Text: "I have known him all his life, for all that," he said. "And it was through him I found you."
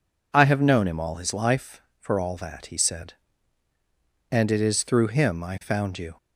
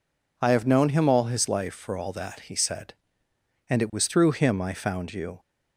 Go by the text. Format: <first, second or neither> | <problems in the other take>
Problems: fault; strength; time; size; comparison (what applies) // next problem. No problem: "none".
second | says "is" for "was"; at 4.5 s